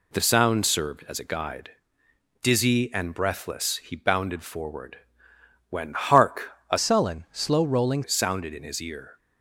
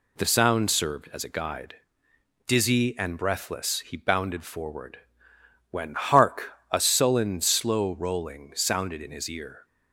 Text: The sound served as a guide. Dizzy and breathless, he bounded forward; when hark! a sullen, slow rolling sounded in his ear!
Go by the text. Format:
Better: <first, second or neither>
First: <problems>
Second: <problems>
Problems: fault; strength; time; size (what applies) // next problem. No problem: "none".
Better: second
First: changes voice from "sullen" to "rolling"; from 6.7 to 8.0 s; 1.3 s long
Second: none